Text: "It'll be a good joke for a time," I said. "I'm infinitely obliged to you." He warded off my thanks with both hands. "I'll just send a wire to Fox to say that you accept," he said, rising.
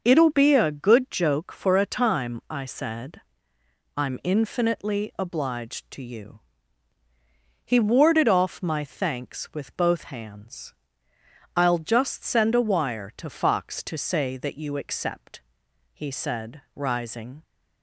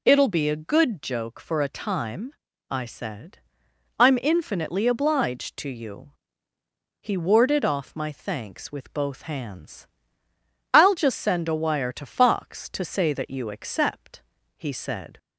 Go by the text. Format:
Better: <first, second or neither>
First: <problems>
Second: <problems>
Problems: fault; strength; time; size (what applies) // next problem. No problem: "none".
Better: first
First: none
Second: stops before "rising"; at 15.1 s